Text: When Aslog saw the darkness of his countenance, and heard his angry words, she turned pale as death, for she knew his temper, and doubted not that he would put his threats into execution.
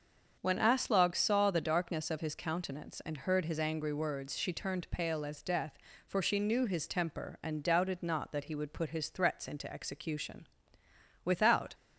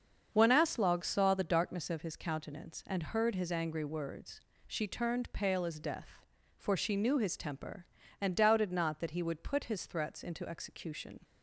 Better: second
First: starts louder than the rest; until 1.4 s; 6.5 dB // goes on to say "Without"; from 11.2 s on; 0.50 s long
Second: starts louder than the rest; until 1.3 s; 7 dB

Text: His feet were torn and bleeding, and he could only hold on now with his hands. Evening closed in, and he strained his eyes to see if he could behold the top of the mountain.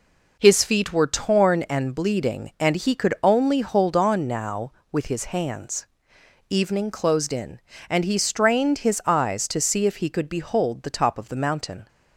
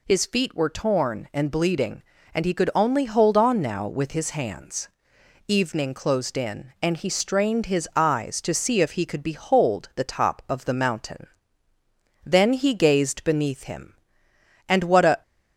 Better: first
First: none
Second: goes on to say "Then he gazed beneath him and what a"; strong; from 12.2 s on; 2.9 s long

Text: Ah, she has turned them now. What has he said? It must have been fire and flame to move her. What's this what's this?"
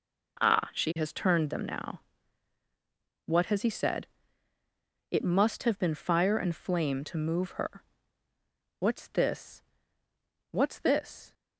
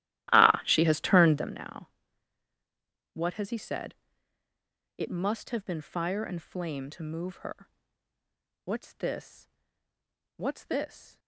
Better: first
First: pauses between "this" and "what's"; noticeable; at 9.6 s; 0.90 s long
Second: starts louder than the rest; strong; until 1.5 s; 15 dB // pauses between "this" and "what's"; noticeable; at 9.4 s; 0.90 s long

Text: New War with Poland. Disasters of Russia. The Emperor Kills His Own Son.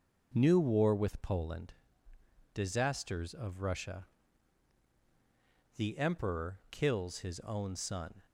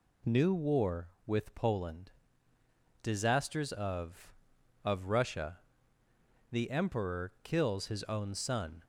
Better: first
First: none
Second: says "of" twice; at 4.8 s

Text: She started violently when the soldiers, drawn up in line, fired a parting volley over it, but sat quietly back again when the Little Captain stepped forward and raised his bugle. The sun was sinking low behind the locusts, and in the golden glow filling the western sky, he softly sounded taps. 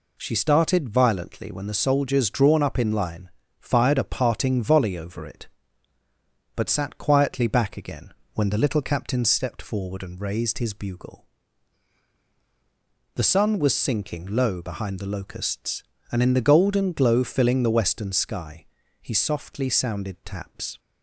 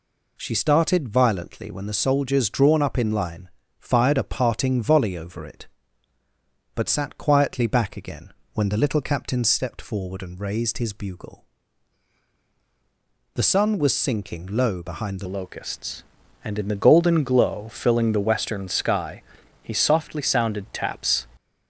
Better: first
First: pauses between "again" and "when"; slight; at 8.1 s; 0.22 s long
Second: pauses between "again" and "when"; slight; at 8.3 s; 0.22 s long // changes voice at "locusts"; from 15.2 s on; 6.0 s long

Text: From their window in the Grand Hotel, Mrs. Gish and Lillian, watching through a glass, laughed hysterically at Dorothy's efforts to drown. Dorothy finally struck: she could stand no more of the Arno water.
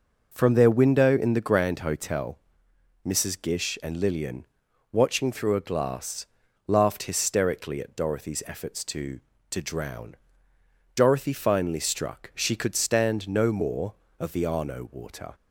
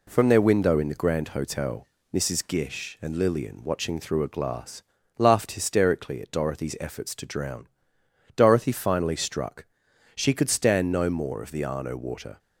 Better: second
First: says "to" twice; at 9.5 s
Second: none

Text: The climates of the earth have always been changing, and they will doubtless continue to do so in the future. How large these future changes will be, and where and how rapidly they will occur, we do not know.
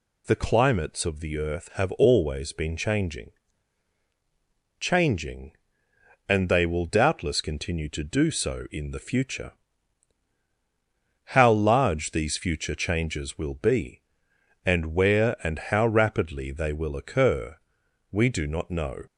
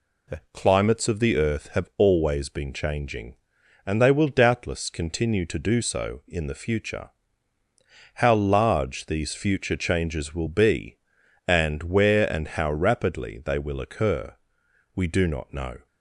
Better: second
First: says "changing" twice; at 4.7 s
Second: none

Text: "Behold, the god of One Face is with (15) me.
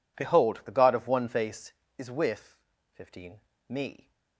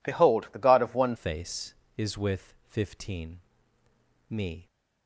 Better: first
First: none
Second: changes voice at "Face"; from 1.1 s on; 3.5 s long

